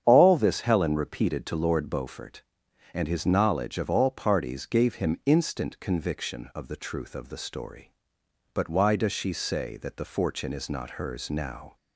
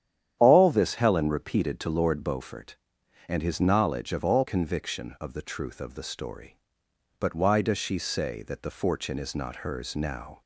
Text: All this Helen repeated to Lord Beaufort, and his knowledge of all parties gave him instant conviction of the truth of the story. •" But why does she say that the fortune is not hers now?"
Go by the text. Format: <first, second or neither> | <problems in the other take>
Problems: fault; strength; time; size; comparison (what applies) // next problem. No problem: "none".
first | starts louder than the rest; strong; until 1.4 s; 10 dB; strong in the first // skips "parties gave him instant"; at 4.4 s